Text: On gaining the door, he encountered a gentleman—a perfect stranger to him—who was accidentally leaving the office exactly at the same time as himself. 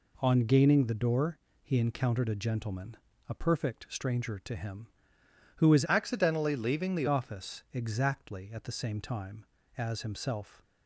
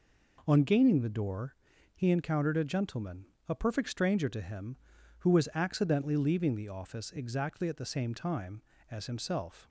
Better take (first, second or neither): second